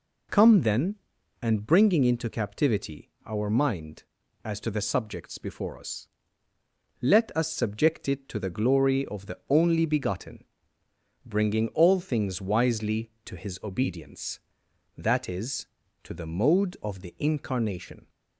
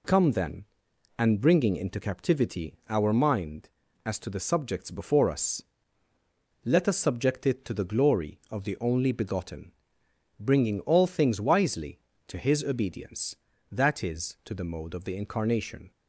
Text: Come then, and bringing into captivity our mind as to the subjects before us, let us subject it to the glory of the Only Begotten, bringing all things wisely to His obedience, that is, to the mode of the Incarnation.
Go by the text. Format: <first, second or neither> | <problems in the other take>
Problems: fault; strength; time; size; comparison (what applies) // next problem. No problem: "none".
neither | pauses between "captivity" and "our"; slight; the same in both